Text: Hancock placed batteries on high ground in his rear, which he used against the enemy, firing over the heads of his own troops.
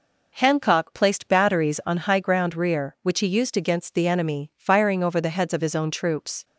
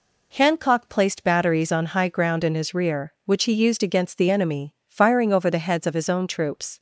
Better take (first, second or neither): second